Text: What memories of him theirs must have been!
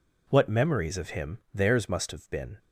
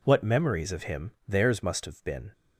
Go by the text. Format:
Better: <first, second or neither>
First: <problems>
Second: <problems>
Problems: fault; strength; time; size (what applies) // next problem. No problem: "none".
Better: neither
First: pauses between "him" and "theirs"; slight; at 1.3 s; 0.17 s long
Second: pauses between "him" and "theirs"; slight; at 1.1 s; 0.18 s long